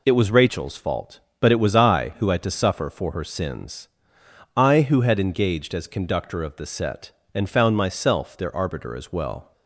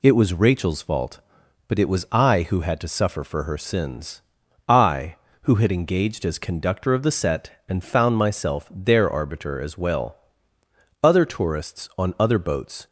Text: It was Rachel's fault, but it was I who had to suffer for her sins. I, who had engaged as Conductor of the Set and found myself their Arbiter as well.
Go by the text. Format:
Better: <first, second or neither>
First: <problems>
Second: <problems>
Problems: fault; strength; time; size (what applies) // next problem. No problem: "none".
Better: first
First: none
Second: goes on to say "Other tourists on other boats"; strong; from 11.0 s on; 1.8 s long